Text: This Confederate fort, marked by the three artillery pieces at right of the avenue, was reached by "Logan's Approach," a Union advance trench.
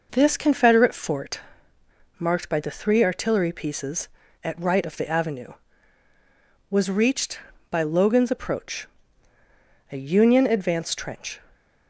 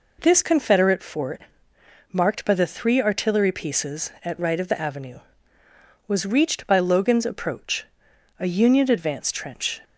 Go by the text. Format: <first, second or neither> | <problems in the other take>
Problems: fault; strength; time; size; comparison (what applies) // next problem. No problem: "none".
neither | none